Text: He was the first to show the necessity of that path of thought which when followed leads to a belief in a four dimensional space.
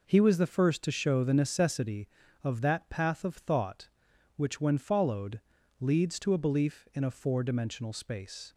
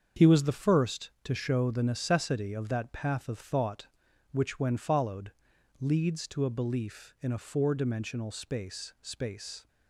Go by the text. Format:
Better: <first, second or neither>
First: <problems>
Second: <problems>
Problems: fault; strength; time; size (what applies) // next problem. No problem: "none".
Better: first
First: pauses between "followed" and "leads"; at 5.3 s; 0.40 s long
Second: starts louder than the rest; strong; until 1.3 s; 7 dB // pauses between "followed" and "leads"; noticeable; at 5.3 s; 0.48 s long // says "space" twice; at 9.0 s